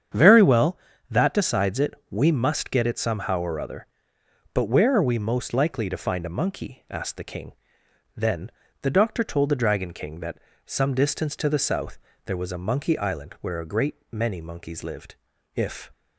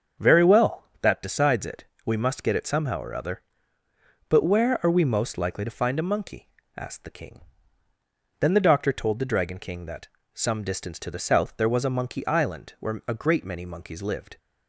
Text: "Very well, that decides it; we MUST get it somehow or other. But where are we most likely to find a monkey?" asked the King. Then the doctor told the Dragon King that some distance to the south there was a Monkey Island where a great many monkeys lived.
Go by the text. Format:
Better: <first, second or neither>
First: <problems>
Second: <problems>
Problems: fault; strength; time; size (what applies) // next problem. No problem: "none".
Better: second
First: starts louder than the rest; strong; until 1.4 s; 8 dB // pauses between "Then" and "the"; slight; at 8.5 s; 0.32 s long // pauses between "that" and "some"; slight; at 10.3 s; 0.30 s long // pauses between "south" and "there"; slight; at 11.9 s; 0.30 s long // pauses between "great" and "many"; slight; at 13.9 s; 0.16 s long // goes on to say "If"; slight; from 15.5 s on; 0.36 s long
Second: starts louder than the rest; until 1.3 s; 7 dB // pauses between "that" and "some"; slight; at 10.0 s; 0.26 s long